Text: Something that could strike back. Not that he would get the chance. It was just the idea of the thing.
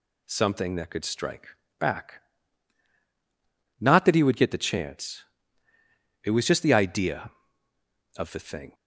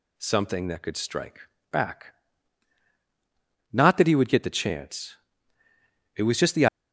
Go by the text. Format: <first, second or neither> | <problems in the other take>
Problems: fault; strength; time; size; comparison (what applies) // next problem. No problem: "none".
first | pauses between "strike" and "back"; slight; at 1.3 s; 0.32 s long; slight in the first // stops before "idea of the thing"; at 6.6 s